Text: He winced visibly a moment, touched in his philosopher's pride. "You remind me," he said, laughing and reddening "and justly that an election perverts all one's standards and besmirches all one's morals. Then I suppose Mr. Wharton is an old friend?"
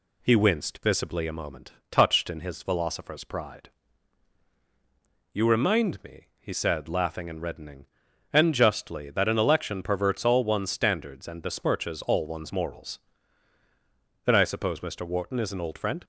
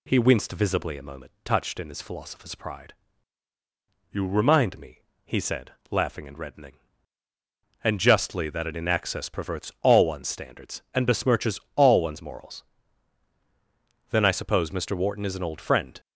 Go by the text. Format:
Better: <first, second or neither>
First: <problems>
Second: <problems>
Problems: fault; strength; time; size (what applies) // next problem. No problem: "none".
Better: first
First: none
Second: says "inaccess" for "election"; at 8.7 s // pauses between "besmirches" and "all"; slight; at 11.5 s; 0.16 s long